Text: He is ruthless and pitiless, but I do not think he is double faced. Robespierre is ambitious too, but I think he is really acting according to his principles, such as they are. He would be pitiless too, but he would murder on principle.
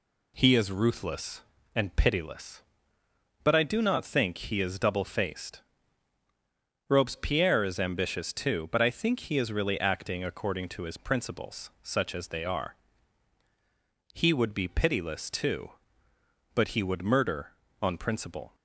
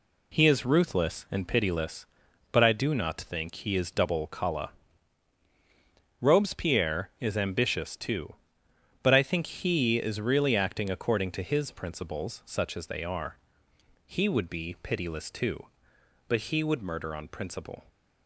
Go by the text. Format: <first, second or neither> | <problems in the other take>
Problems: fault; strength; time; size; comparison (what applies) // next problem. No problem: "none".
first | says "kala" for "faced"; at 4.2 s